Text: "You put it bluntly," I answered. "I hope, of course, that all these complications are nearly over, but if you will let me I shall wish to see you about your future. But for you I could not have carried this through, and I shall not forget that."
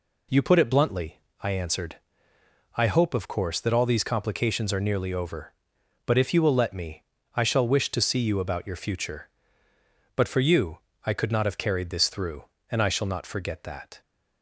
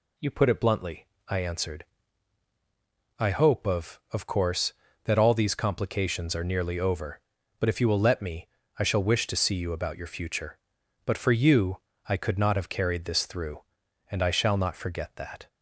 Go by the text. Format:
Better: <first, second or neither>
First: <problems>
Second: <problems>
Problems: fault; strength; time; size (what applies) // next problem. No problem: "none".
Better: first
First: pauses between "me" and "I"; slight; at 7.0 s; 0.32 s long // pauses between "you" and "I"; slight; at 10.8 s; 0.24 s long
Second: says "of" twice; at 4.1 s // pauses between "me" and "I"; slight; at 8.4 s; 0.32 s long // pauses between "you" and "I"; slight; at 11.8 s; 0.28 s long